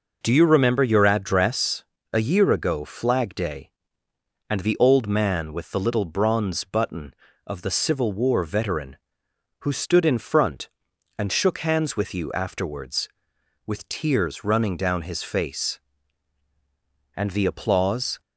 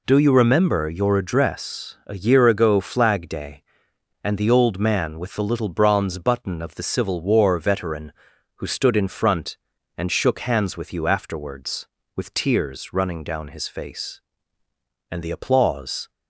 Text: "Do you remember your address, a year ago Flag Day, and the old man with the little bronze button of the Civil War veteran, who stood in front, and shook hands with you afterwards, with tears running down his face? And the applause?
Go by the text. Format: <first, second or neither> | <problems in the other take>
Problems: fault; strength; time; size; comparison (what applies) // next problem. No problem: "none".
neither | none